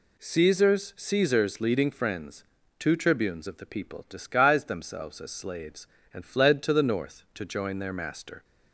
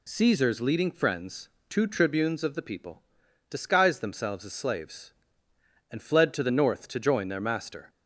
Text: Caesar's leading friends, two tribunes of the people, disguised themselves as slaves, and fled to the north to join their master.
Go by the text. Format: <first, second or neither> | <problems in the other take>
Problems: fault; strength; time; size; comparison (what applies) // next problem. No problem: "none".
second | says "Caesar's" twice; at 0.9 s